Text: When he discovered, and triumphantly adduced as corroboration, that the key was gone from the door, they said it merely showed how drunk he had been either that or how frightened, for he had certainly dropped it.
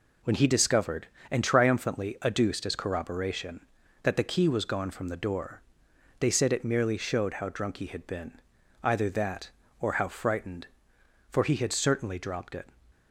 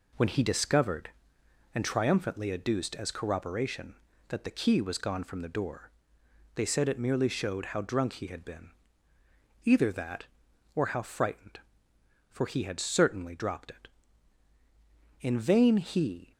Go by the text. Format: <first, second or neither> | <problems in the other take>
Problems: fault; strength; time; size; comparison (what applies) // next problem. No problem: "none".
first | pauses between "been" and "either"; noticeable; at 8.6 s; 0.96 s long; noticeable in the first // goes on to say "In vain he"; noticeable; from 15.2 s on; 1.1 s long